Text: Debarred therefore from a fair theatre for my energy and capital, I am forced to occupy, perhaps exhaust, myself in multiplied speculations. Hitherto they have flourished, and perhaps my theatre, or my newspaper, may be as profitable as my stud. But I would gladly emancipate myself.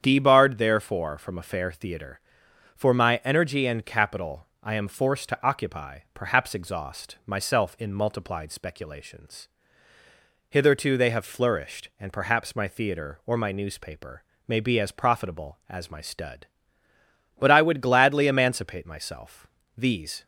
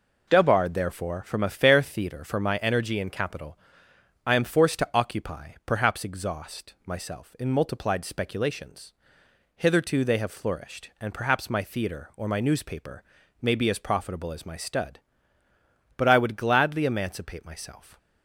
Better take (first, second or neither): second